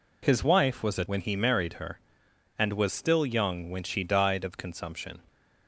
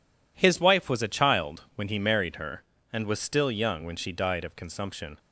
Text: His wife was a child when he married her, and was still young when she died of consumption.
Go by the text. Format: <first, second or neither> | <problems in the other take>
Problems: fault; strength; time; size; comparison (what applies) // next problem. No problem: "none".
second | skips "child"; at 1.0 s